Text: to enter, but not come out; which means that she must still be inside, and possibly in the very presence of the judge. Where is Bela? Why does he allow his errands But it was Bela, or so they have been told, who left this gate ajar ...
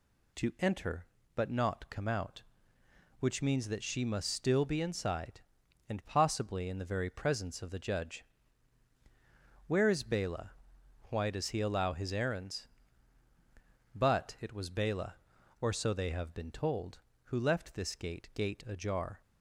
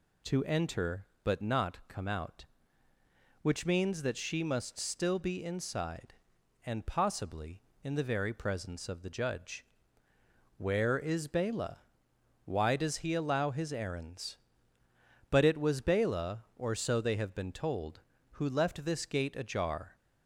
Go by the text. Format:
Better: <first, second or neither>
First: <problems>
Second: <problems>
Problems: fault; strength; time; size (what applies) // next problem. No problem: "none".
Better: second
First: says "gate" twice; at 18.3 s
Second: none